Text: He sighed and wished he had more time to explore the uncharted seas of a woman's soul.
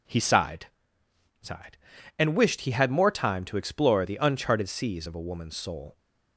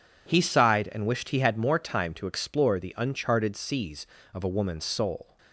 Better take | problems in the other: second | says "sighed" twice; at 1.4 s

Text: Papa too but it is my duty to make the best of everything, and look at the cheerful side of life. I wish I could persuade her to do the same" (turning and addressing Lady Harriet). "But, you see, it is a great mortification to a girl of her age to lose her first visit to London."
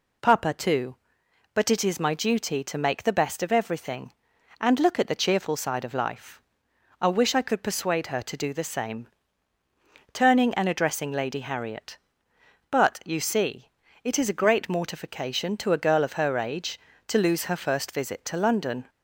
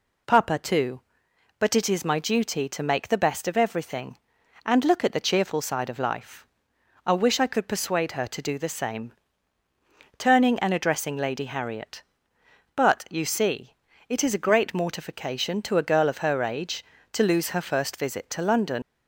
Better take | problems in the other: first | leaves "London" unfinished; at 18.8 s; 120 ms

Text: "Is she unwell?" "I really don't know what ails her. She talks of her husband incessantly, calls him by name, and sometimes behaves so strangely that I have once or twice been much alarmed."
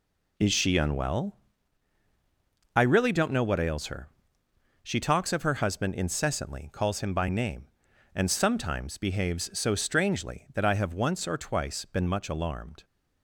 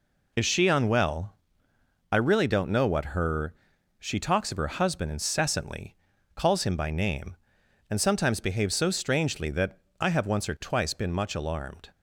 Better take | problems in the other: first | skips "ails"; at 3.1 s // pauses between "that" and "I"; slight; at 9.7 s; 0.22 s long

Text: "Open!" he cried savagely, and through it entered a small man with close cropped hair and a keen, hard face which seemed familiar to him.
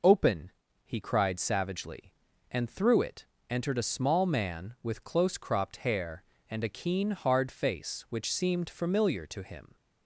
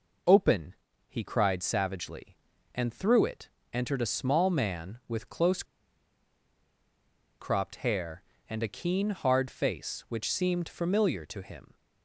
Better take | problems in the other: first | pauses between "it" and "entered"; slight; at 3.4 s; 0.24 s long; slight in the first // pauses between "close" and "cropped"; strong; at 5.6 s; 1.7 s long

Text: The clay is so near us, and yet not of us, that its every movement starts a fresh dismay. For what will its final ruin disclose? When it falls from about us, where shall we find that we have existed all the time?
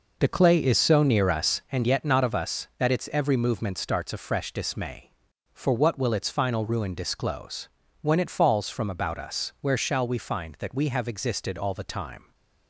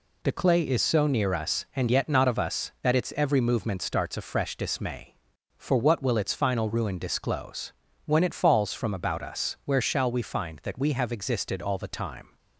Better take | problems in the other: second | starts louder than the rest; noticeable; until 1.7 s; 5 dB

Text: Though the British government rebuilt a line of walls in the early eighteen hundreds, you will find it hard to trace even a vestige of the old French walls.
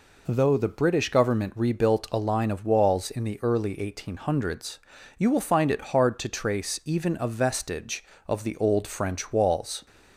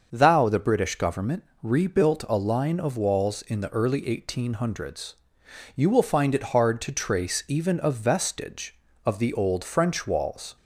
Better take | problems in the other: first | starts louder than the rest; until 1.1 s; 6.5 dB // says "Thou" for "Though"; at 0.1 s // pauses between "government" and "rebuilt"; slight; at 1.4 s; 0.20 s long

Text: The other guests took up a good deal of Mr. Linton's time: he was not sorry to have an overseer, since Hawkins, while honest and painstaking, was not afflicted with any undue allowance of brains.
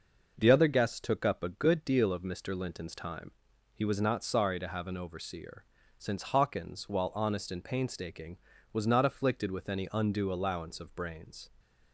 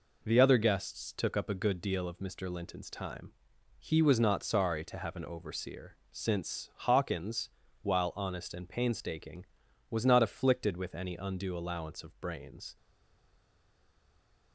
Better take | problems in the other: first | stays silent after the last word; noticeable; from 12.7 s on; 1.8 s long

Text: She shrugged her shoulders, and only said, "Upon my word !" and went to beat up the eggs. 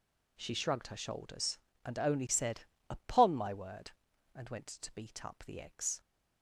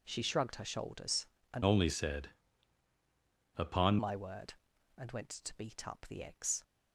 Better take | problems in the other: first | changes voice from "only" to "Upon"; from 1.6 to 3.9 s; 2.3 s long

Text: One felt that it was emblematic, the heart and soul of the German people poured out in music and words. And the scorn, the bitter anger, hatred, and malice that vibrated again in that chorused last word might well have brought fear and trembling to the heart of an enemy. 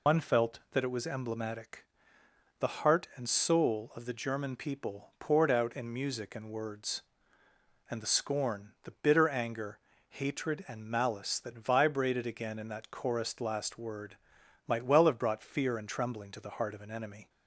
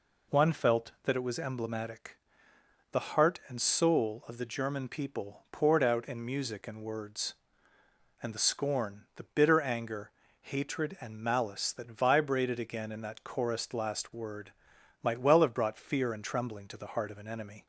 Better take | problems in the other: second | loses the start of "One"; at 0.0 s; 90 ms // pauses between "word" and "might"; noticeable; at 14.1 s; 0.50 s long; noticeable in the second

